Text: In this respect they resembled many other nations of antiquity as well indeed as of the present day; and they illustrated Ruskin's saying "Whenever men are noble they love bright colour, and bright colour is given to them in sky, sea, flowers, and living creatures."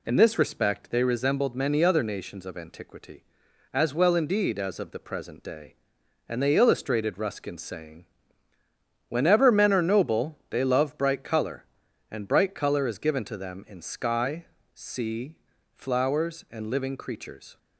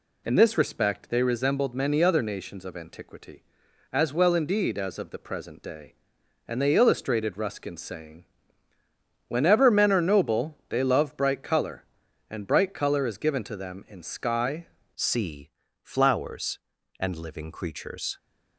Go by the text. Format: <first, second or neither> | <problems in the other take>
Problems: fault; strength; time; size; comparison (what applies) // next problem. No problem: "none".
first | pauses between "saying" and "Whenever"; at 8.2 s; 1.0 s long; also in the first // changes voice at "sea"; from 14.9 s on; 3.2 s long